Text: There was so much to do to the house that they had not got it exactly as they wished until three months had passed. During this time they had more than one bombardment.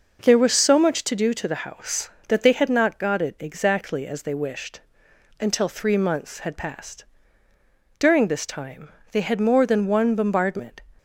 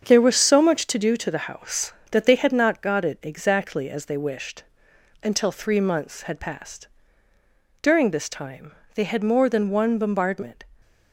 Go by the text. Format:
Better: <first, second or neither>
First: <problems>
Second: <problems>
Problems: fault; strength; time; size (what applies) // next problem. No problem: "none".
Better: first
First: pauses between "wished" and "until"; noticeable; at 4.8 s; 0.60 s long // pauses between "time" and "they"; slight; at 8.9 s; 0.22 s long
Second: gets quieter; throughout; 7 dB // pauses between "wished" and "until"; noticeable; at 4.6 s; 0.60 s long // pauses between "time" and "they"; slight; at 8.7 s; 0.22 s long